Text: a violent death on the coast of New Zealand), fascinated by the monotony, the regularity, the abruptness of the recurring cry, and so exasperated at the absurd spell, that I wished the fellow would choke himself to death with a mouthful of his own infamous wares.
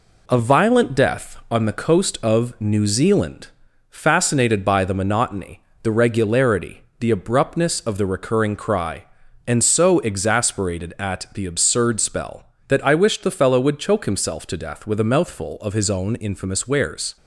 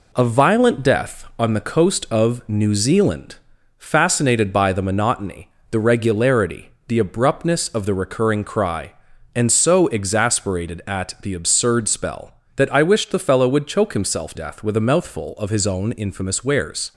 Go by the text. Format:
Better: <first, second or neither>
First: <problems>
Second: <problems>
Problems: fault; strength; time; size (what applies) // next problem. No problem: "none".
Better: first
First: none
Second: skips "to"; at 14.3 s